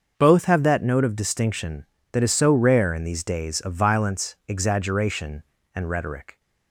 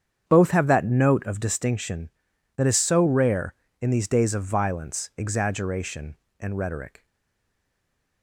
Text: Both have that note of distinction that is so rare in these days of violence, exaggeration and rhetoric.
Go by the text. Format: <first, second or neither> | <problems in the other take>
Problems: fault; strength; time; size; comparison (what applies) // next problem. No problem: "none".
first | starts louder than the rest; strong; until 1.2 s; 8 dB; also in the first // stays silent after the last word; noticeable; from 7.0 s on; 1.2 s long